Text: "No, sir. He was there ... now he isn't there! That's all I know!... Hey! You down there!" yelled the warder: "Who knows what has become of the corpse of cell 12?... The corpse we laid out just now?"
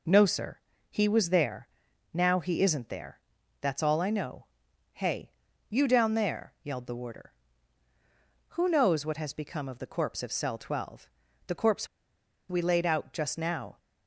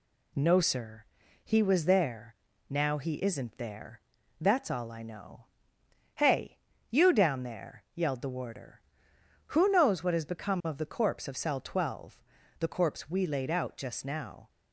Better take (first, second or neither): second